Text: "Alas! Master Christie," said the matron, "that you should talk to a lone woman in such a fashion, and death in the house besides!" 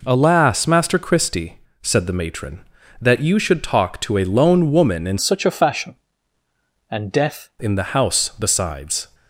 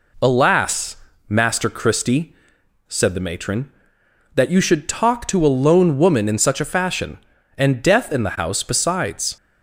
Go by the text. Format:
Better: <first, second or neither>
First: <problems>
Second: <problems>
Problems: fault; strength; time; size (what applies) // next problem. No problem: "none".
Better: second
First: changes voice from "such" to "death"; from 5.1 to 7.5 s; 2.4 s long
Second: none